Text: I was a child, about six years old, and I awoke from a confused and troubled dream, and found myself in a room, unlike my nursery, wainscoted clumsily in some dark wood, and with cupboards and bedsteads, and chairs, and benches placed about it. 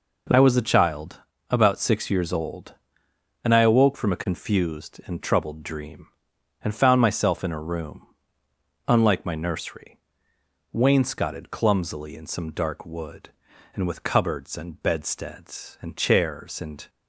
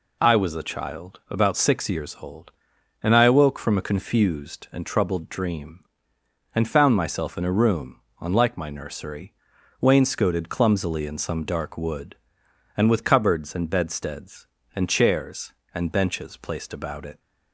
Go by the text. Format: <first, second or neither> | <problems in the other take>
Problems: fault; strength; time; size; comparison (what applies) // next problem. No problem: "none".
second | stops before "benches placed about it"; at 16.8 s